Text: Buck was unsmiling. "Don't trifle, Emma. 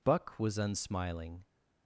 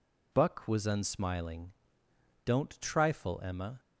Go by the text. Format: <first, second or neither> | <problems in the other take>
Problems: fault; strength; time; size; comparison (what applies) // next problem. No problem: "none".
second | stops before "Don't trifle Emma"; at 1.4 s